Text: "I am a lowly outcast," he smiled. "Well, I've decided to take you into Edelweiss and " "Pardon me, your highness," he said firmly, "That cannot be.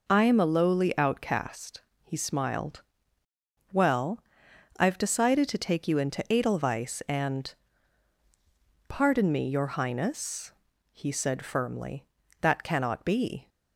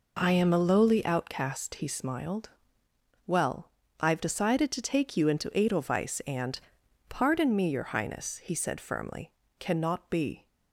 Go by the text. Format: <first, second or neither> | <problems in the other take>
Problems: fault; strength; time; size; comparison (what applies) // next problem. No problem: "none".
first | skips "That"; at 9.4 s